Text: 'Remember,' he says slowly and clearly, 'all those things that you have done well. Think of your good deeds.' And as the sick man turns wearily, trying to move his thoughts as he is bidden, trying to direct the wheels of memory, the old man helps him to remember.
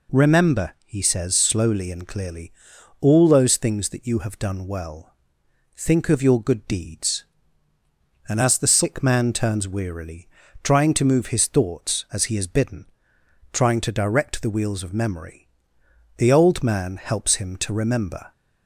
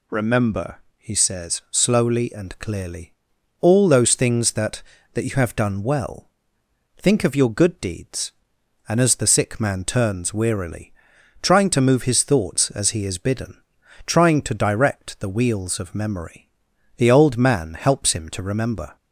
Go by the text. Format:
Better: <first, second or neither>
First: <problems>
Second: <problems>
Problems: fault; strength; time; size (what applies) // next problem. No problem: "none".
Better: first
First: none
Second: says "that" twice; at 5.1 s